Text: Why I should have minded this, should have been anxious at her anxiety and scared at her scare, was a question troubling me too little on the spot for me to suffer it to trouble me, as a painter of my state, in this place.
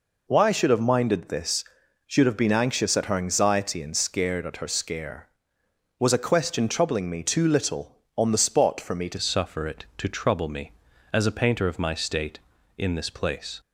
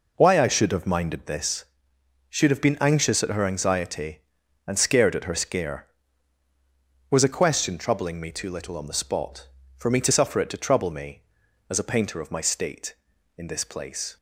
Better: second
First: changes voice at "suffer"; from 9.1 s on; 4.4 s long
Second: none

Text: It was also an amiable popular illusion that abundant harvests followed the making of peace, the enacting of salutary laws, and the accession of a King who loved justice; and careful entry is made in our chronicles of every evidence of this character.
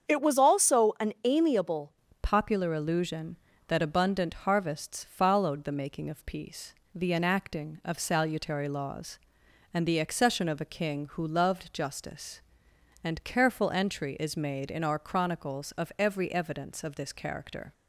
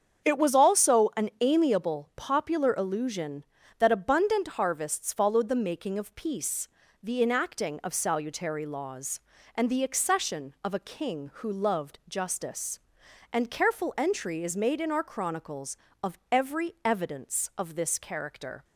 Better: second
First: starts louder than the rest; strong; until 1.2 s; 7.5 dB // changes voice at "popular"; from 2.2 s on; 15.5 s long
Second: starts louder than the rest; strong; until 1.4 s; 7.5 dB

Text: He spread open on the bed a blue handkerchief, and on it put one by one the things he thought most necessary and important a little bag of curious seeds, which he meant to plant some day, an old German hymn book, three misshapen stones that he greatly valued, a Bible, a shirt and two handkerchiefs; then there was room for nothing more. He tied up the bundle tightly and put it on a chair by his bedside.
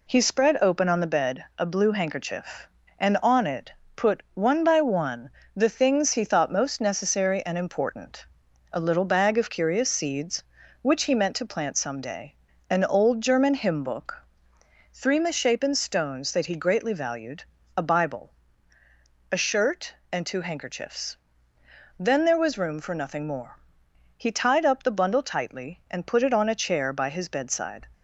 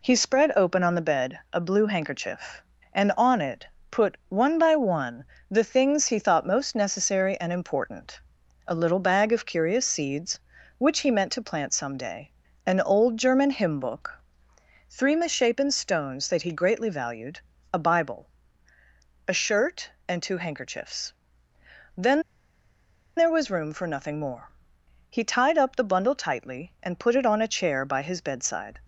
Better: first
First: pauses between "it" and "put"; slight; at 3.7 s; 0.24 s long // pauses between "one" and "the"; slight; at 5.2 s; 0.26 s long // pauses between "important" and "a"; noticeable; at 8.2 s; 0.48 s long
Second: pauses between "it" and "put"; slight; at 3.6 s; 0.24 s long // pauses between "one" and "the"; slight; at 5.2 s; 0.26 s long // pauses between "important" and "a"; noticeable; at 8.1 s; 0.48 s long // pauses between "then" and "there"; noticeable; at 22.2 s; 0.96 s long

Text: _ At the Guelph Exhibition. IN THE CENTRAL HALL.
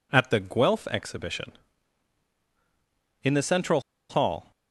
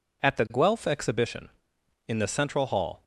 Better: second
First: pauses between "CENTRAL" and "HALL"; slight; at 3.8 s; 0.28 s long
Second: none

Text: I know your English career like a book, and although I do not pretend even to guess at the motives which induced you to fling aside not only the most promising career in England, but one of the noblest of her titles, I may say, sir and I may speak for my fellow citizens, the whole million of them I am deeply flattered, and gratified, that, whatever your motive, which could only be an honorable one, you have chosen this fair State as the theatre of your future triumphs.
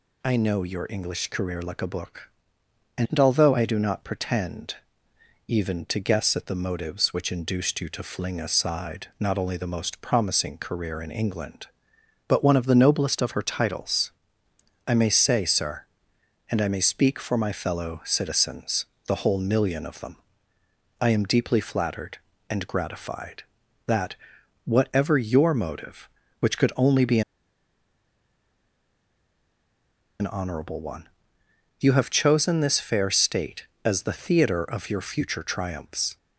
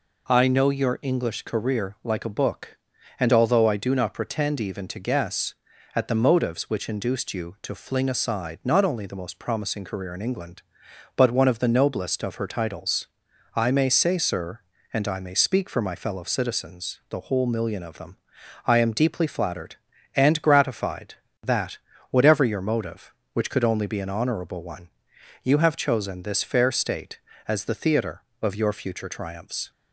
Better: second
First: pauses between "pretend" and "even"; noticeable; at 4.7 s; 0.72 s long // pauses between "them" and "I"; noticeable; at 20.1 s; 0.84 s long // pauses between "be" and "an"; strong; at 27.2 s; 2.9 s long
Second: pauses between "them" and "I"; noticeable; at 18.1 s; 0.48 s long

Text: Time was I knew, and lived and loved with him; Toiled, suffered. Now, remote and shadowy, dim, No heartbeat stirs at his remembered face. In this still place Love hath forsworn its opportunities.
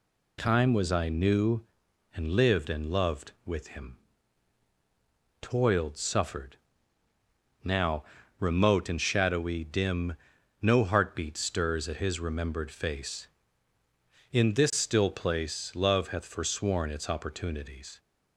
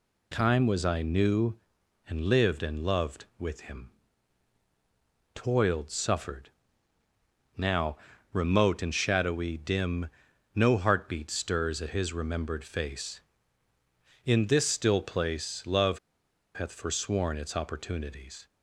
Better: first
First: none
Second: pauses between "Love" and "hath"; noticeable; at 15.9 s; 0.56 s long

